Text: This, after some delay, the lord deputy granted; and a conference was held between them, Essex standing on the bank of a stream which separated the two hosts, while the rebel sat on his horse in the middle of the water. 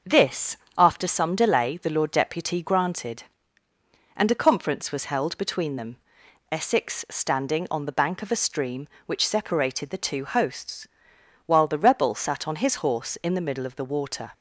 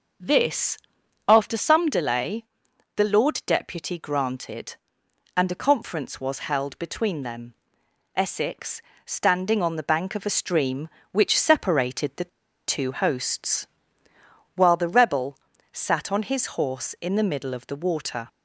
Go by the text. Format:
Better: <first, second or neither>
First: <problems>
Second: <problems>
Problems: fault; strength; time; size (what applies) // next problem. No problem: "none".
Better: first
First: starts louder than the rest; until 1.2 s; 6 dB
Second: starts louder than the rest; noticeable; until 1.7 s; 6 dB // pauses between "Essex" and "standing"; slight; at 8.8 s; 0.20 s long // pauses between "the" and "two"; at 12.2 s; 0.38 s long // pauses between "rebel" and "sat"; slight; at 15.3 s; 0.34 s long